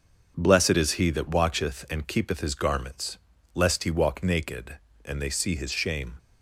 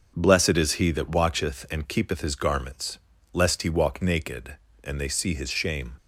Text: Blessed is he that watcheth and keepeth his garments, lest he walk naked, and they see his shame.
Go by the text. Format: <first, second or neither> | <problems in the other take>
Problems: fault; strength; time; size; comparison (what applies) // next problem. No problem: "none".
neither | starts louder than the rest; the same in both